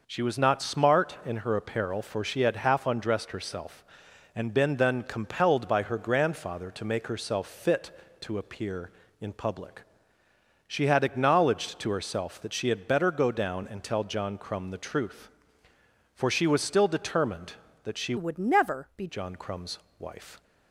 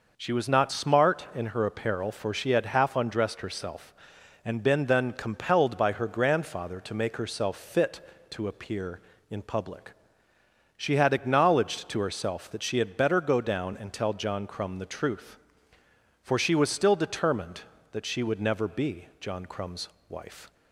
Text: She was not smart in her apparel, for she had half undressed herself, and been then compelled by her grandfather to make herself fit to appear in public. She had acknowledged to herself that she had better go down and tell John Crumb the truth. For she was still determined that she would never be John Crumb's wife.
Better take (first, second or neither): second